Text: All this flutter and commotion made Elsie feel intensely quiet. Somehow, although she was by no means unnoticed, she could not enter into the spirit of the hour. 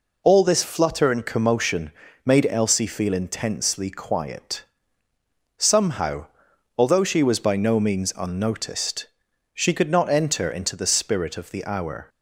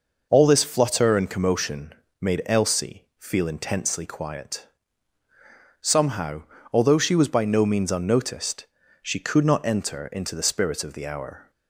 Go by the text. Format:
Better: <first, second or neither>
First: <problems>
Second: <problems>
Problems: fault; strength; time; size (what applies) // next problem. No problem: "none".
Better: neither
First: pauses between "commotion" and "made"; slight; at 1.9 s; 0.34 s long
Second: pauses between "commotion" and "made"; slight; at 1.9 s; 0.26 s long